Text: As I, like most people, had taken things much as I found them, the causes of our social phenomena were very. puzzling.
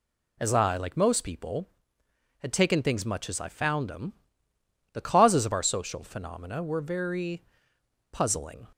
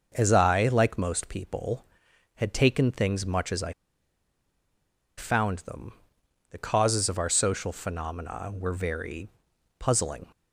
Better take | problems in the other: first | pauses between "I" and "found"; strong; at 3.7 s; 1.4 s long

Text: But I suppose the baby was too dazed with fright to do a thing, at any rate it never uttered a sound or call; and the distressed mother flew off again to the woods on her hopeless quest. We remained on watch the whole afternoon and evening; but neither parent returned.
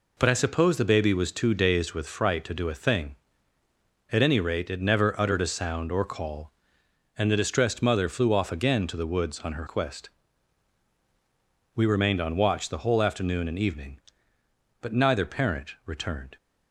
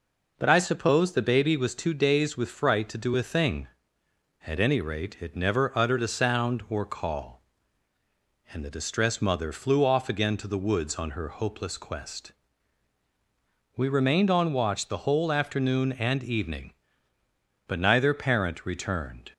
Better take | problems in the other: second | skips "hopeless"; at 9.6 s

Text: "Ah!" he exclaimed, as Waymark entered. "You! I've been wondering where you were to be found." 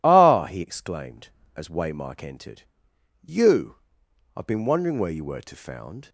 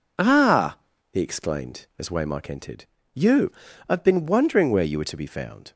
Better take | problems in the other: second | skips "be"; at 5.5 s

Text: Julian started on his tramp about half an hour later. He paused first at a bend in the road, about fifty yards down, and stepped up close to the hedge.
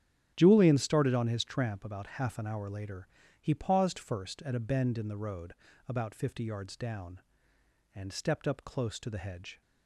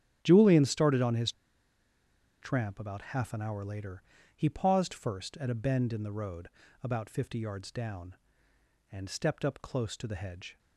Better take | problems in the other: first | starts louder than the rest; strong; until 1.2 s; 9 dB; strong in the first // pauses between "his" and "tramp"; at 1.3 s; 1.0 s long

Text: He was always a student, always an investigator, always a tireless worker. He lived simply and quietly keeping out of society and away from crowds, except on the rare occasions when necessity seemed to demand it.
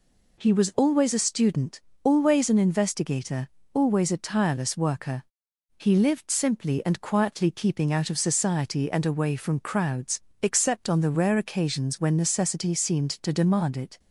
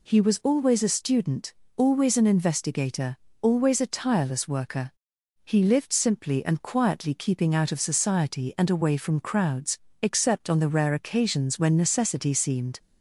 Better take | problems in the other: first | stops before "to demand it"; at 12.7 s

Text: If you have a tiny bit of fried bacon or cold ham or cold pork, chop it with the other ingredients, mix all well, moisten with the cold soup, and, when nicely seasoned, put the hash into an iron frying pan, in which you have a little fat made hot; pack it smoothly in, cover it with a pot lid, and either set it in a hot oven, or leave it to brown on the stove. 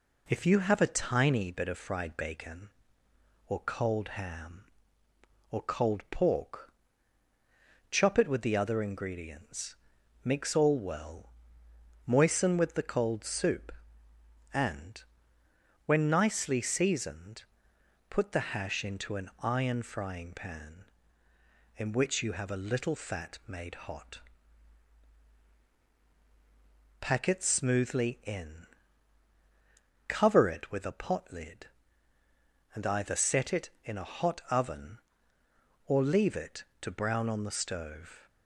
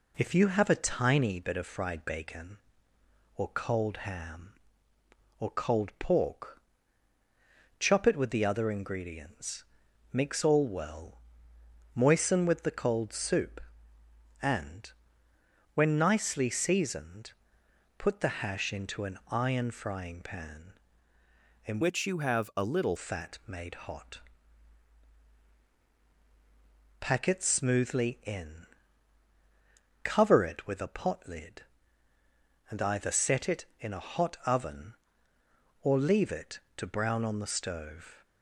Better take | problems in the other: first | changes voice from "which" to "little"; from 21.8 to 22.9 s; 1.1 s long

